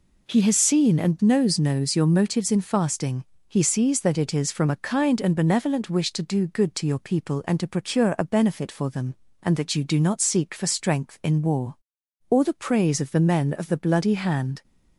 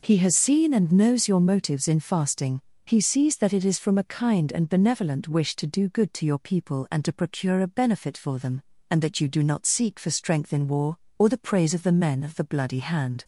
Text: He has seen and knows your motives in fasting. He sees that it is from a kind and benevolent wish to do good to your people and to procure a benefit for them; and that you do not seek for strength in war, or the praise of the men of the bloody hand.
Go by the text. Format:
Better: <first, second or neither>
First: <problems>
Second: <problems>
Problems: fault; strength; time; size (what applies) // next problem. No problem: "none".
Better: second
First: says "knows" twice; at 1.5 s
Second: none